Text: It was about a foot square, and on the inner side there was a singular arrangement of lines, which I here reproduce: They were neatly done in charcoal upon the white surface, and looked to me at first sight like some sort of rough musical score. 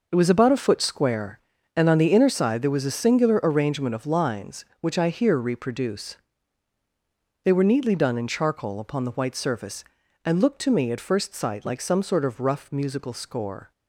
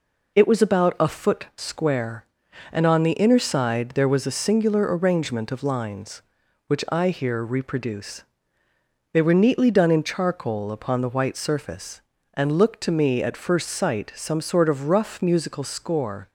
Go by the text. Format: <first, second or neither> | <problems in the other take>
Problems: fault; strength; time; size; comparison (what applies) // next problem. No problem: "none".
first | skips "like"; at 14.1 s